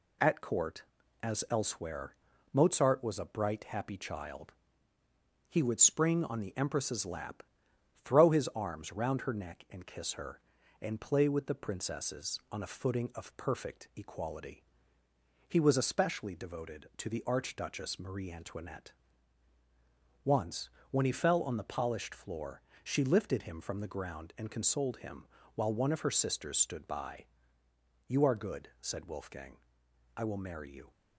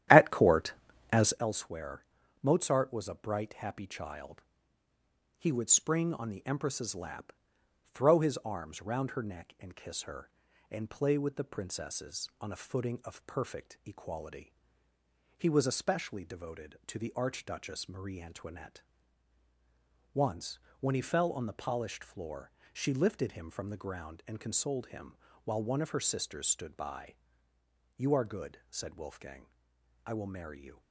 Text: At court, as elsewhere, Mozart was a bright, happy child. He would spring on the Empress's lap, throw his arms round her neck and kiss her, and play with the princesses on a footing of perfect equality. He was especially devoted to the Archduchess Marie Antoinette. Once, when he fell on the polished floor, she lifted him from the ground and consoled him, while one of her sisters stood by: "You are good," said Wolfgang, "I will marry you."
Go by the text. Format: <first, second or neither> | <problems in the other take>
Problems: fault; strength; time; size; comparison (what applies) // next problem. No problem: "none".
first | starts louder than the rest; strong; until 1.4 s; 12 dB